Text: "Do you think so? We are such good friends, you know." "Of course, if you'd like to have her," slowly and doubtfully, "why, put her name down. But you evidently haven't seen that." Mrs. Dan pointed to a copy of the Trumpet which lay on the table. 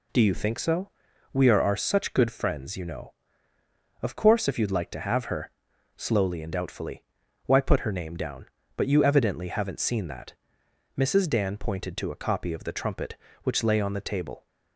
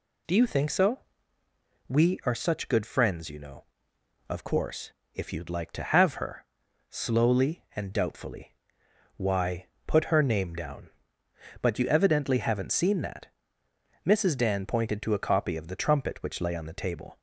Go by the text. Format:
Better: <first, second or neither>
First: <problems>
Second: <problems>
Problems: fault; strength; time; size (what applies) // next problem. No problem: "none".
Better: second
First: says "are" twice; at 1.6 s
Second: none